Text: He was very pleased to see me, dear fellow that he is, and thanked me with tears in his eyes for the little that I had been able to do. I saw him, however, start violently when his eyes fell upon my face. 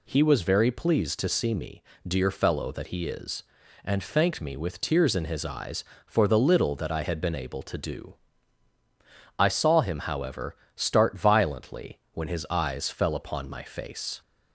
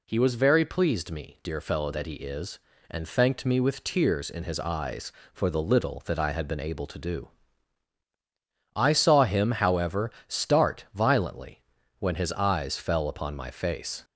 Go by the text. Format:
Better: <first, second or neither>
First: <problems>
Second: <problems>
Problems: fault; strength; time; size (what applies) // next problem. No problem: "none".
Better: first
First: none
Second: skips "to see"; at 1.1 s // pauses between "violently" and "when"; at 11.6 s; 0.38 s long